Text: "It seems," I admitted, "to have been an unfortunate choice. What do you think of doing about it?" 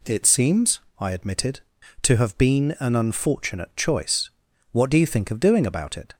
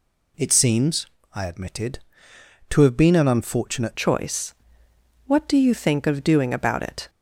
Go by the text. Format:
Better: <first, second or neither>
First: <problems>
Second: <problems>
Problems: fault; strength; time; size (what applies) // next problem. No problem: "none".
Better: first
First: none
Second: changes voice at "choice"; from 3.9 s on; 3.1 s long